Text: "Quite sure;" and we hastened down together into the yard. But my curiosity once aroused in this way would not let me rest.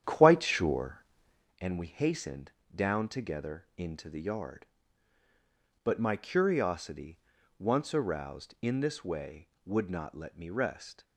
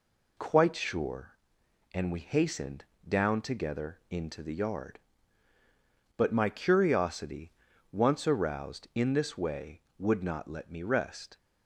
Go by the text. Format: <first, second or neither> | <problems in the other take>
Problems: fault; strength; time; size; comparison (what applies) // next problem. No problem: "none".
second | starts louder than the rest; strong; until 1.6 s; 9.5 dB // pauses between "hastened" and "down"; slight; at 2.4 s; 0.24 s long; slight in the second // pauses between "curiosity" and "once"; at 7.1 s; 0.40 s long; also in the second